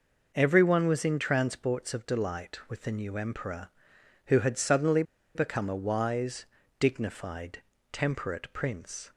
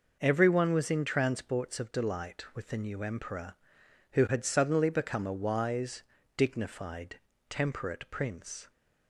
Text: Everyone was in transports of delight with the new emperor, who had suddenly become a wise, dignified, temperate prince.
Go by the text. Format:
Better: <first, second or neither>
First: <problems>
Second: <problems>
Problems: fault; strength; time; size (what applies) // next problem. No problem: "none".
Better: second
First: pauses between "suddenly" and "become"; slight; at 5.0 s; 0.32 s long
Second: none